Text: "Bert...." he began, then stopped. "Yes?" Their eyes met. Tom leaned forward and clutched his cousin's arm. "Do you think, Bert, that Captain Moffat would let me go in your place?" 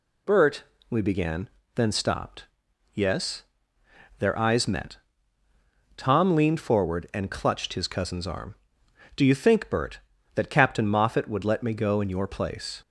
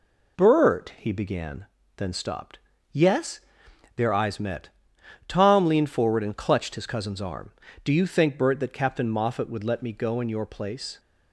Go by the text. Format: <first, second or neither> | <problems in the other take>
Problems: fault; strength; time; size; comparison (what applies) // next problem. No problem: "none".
second | says "we" for "he"; at 0.8 s